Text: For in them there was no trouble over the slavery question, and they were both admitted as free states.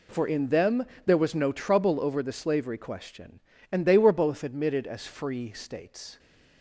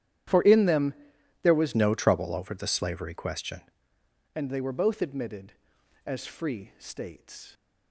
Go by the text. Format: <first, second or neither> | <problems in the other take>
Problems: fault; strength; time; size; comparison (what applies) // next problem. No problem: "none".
first | starts louder than the rest; strong; until 1.7 s; 11 dB // pauses between "them" and "there"; noticeable; at 0.9 s; 0.50 s long; slight in the first // changes voice from "no" to "question"; from 1.7 to 3.6 s; 1.9 s long